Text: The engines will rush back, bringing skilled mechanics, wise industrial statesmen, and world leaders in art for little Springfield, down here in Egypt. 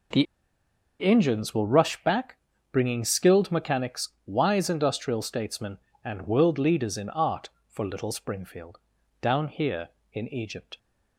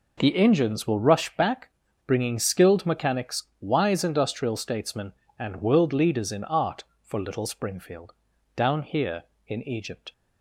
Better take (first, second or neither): second